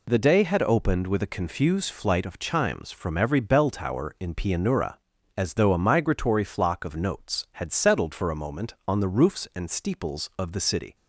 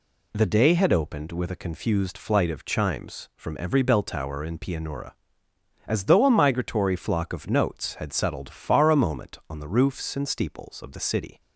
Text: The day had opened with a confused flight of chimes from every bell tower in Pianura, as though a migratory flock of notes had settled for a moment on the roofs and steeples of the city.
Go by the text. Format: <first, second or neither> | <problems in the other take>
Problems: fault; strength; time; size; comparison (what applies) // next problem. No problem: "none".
first | says "far" for "for"; at 8.4 s